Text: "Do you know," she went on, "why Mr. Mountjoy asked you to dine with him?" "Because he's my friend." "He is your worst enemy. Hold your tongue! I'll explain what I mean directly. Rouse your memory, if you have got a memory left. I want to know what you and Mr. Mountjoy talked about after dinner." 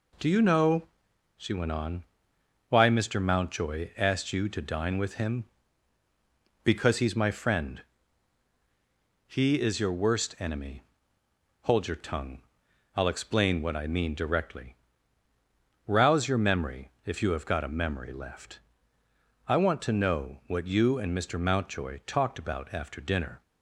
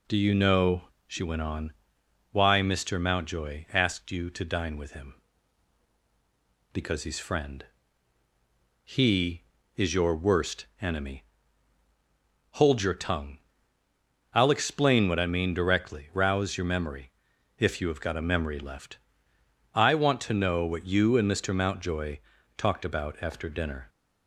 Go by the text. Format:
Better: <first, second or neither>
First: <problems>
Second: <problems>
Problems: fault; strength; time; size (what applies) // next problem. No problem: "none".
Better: first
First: none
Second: skips "my"; at 7.1 s // pauses between "Mountjoy" and "talked"; at 22.1 s; 0.38 s long